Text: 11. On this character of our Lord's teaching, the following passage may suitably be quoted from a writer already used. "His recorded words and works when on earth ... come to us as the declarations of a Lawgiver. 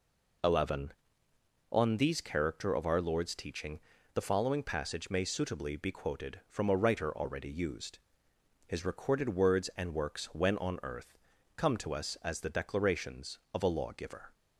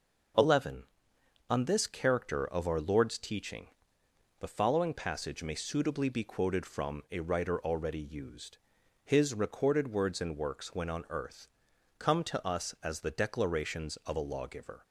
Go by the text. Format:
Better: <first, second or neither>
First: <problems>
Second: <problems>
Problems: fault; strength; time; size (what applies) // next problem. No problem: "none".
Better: second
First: says "these" for "this"; at 1.9 s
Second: none